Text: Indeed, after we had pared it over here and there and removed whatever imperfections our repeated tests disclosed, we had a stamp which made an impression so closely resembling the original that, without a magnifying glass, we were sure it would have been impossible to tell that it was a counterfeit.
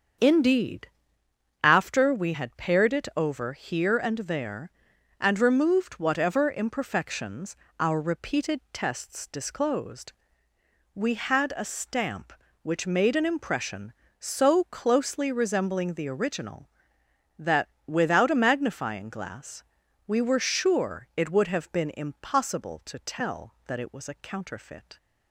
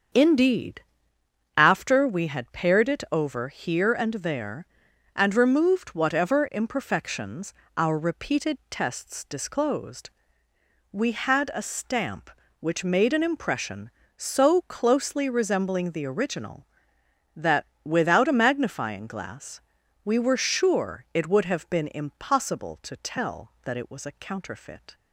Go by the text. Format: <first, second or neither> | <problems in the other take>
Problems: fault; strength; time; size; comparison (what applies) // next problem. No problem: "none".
neither | starts louder than the rest; the same in both // pauses between "imperfections" and "our"; slight; the same in both